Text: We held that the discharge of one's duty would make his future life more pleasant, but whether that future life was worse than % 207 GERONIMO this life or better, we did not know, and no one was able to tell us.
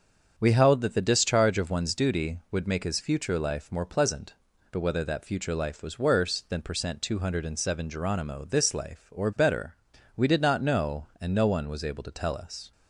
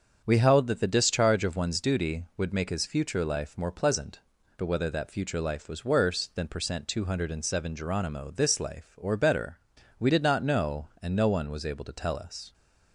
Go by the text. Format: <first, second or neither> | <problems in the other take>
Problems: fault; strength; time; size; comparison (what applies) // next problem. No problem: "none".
neither | starts louder than the rest; the same in both